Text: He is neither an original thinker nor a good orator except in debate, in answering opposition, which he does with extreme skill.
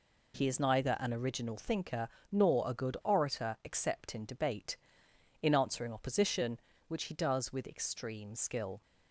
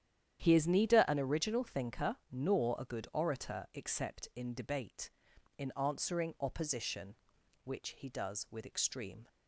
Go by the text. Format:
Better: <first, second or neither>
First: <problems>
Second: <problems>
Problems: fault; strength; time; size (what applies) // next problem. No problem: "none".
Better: first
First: pauses between "thinker" and "nor"; slight; at 2.0 s; 0.20 s long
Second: starts louder than the rest; strong; until 1.4 s; 10 dB // pauses between "thinker" and "nor"; slight; at 2.1 s; 0.16 s long // stops before "skill"; at 9.2 s